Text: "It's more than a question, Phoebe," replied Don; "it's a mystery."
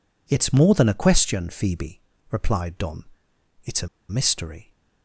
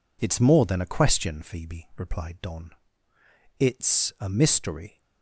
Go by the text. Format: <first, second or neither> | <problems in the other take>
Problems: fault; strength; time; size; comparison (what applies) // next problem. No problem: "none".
second | pauses between "a" and "mystery"; slight; at 3.8 s; 0.22 s long